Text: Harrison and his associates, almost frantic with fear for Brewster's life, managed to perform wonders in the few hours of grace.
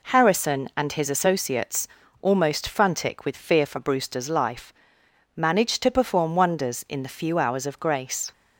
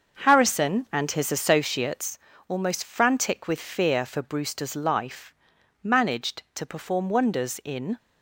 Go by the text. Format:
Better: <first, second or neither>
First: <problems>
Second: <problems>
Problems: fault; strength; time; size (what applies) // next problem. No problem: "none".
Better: first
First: none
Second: starts louder than the rest; until 1.3 s; 6.5 dB // stops before "the few hours of grace"; at 7.9 s